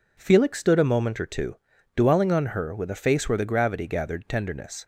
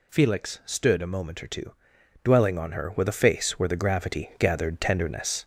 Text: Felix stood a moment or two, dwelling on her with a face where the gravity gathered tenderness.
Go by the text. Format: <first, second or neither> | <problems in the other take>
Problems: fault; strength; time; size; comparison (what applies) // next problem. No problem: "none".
first | gets louder; slight; throughout; 2.5 dB